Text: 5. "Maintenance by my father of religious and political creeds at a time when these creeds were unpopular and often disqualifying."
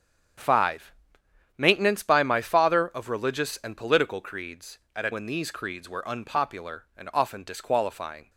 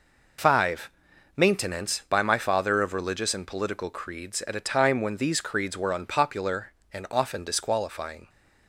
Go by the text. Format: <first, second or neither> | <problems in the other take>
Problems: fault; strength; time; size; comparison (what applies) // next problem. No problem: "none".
second | starts louder than the rest; strong; until 2.0 s; 7.5 dB // skips "time"; at 5.1 s